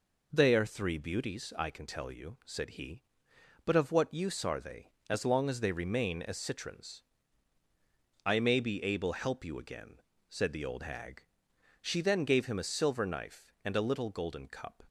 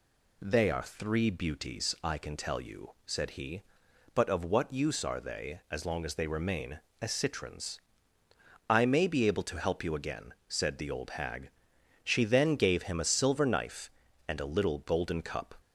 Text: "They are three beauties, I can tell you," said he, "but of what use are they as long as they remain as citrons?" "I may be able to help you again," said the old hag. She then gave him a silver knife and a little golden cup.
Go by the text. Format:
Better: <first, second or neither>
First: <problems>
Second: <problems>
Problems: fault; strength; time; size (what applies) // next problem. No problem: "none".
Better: second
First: skips "to"; at 9.1 s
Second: none